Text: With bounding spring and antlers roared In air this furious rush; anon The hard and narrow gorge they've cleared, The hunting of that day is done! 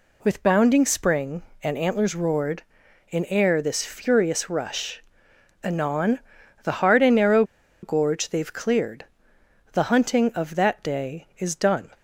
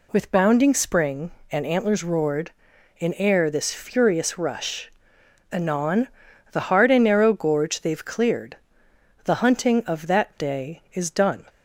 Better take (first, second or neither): second